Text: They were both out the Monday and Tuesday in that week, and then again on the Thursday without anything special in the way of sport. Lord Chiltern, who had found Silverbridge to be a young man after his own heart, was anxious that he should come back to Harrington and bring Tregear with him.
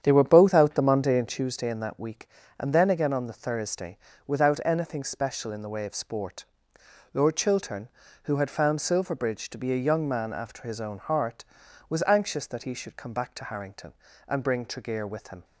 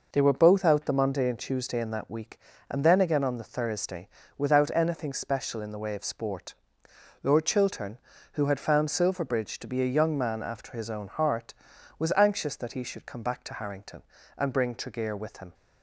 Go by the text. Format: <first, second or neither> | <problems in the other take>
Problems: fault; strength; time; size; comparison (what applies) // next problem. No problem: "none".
second | starts louder than the rest; strong; until 1.4 s; 8.5 dB // pauses between "Thursday" and "without"; slight; at 3.9 s; 0.28 s long; slight in the second